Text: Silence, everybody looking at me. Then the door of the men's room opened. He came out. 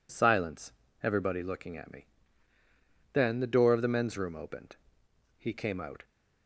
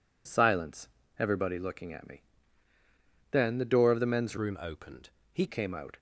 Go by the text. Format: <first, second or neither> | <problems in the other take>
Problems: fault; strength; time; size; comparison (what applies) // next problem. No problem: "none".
first | changes voice from "room" to "He"; from 4.3 to 5.4 s; 1.1 s long